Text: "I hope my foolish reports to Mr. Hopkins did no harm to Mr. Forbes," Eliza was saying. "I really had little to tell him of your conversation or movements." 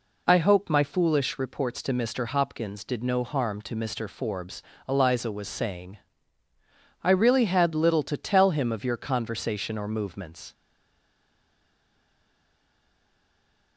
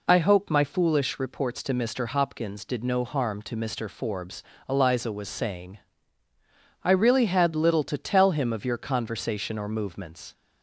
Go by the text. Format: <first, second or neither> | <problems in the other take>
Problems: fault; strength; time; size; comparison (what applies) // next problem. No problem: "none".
second | stays silent after the last word; strong; from 10.5 s on; 3.2 s long